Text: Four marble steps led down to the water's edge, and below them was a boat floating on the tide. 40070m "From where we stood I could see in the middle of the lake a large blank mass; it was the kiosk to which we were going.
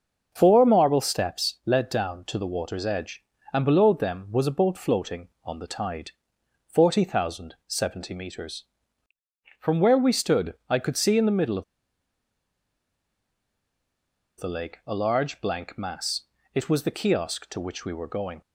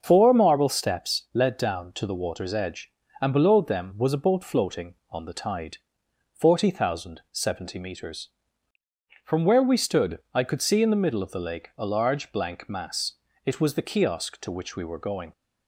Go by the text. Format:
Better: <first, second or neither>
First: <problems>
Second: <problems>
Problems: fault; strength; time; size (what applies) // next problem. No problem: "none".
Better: second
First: starts louder than the rest; until 1.3 s; 6 dB // pauses between "stood" and "I"; slight; at 10.5 s; 0.16 s long // pauses between "of" and "the"; strong; at 11.6 s; 2.7 s long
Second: starts louder than the rest; noticeable; until 1.0 s; 6 dB // pauses between "stood" and "I"; slight; at 10.1 s; 0.16 s long